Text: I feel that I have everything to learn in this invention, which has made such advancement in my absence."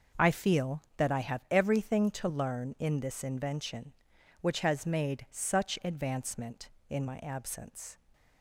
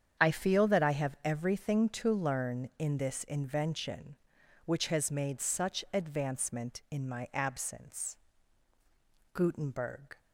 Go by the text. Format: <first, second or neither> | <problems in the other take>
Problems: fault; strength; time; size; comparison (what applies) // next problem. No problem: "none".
first | starts louder than the rest; strong; until 1.3 s; 8 dB // goes on to say "Gutenberg"; noticeable; from 9.3 s on; 0.86 s long